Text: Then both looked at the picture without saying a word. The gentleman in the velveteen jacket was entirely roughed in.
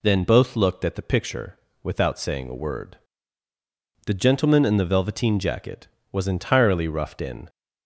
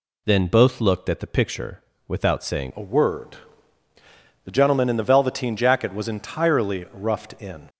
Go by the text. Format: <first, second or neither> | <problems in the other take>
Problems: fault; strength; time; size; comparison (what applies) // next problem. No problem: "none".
first | pauses between "picture" and "without"; slight; at 1.8 s; 0.26 s long; slight in the first // changes voice at "a"; from 2.7 s on; 4.9 s long